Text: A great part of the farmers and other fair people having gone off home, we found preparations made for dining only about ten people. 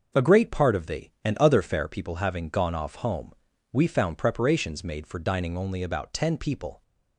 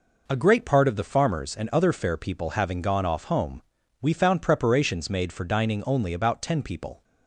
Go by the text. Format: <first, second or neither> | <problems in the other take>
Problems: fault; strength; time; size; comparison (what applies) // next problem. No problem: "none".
second | starts louder than the rest; noticeable; until 1.2 s; 6 dB // skips "farmers"; at 1.1 s